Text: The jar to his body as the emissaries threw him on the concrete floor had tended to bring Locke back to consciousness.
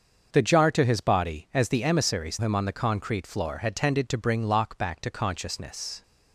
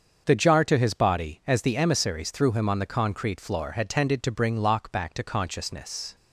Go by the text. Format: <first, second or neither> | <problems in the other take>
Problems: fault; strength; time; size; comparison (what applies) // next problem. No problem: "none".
second | starts louder than the rest; until 1.3 s; 6.5 dB; also in the second // skips "threw"; at 2.3 s